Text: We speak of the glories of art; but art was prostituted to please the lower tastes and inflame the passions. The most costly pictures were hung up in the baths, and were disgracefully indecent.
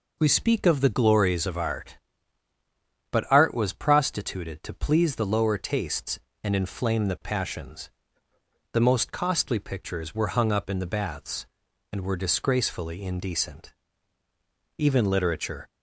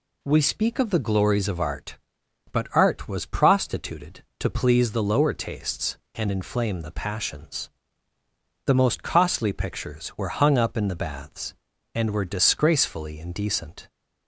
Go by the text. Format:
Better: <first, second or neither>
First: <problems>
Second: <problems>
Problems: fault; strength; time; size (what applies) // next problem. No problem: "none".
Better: second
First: goes on to say "Even literature"; noticeable; from 14.7 s on; 0.90 s long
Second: none